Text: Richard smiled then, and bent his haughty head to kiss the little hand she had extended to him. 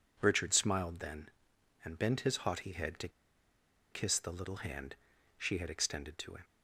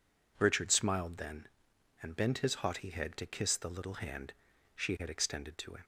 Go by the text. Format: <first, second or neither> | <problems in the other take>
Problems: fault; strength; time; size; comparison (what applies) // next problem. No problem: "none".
second | pauses between "to" and "kiss"; noticeable; at 3.0 s; 0.83 s long // pauses between "hand" and "she"; at 4.9 s; 0.40 s long; also in the second